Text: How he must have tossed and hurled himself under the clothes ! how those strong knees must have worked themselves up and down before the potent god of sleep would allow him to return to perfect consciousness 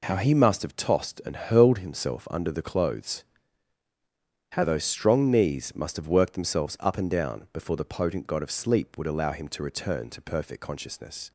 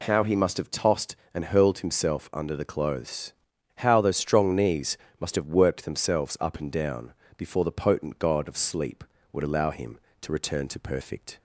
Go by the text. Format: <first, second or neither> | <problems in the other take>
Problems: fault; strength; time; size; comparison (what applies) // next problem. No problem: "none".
first | pauses between "knees" and "must"; slight; at 4.9 s; 0.22 s long // pauses between "down" and "before"; slight; at 7.1 s; 0.24 s long // stops before "consciousness"; at 11.3 s